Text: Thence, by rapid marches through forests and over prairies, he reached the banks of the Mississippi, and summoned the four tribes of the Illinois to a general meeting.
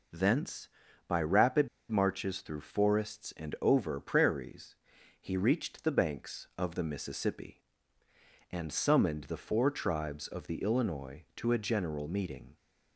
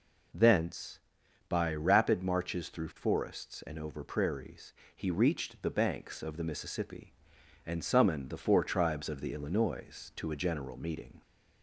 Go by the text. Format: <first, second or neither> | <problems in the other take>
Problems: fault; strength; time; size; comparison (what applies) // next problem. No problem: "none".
second | pauses between "rapid" and "marches"; slight; at 1.6 s; 0.23 s long